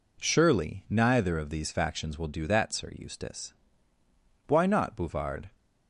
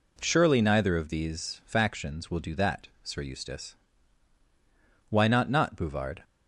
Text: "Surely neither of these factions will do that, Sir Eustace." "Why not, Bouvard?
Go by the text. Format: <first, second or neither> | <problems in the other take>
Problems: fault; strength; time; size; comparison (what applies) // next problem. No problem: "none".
first | says "not" twice; at 5.4 s